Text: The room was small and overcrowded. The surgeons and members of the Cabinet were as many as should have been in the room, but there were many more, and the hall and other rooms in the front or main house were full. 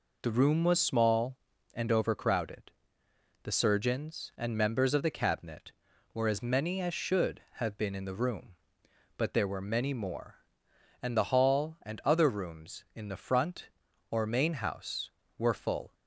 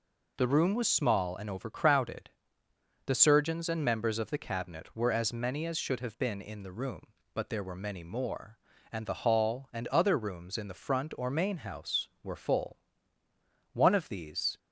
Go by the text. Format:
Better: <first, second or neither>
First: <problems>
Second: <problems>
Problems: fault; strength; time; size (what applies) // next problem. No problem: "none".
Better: first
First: none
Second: goes on to say "One of these"; noticeable; from 13.7 s on; 0.84 s long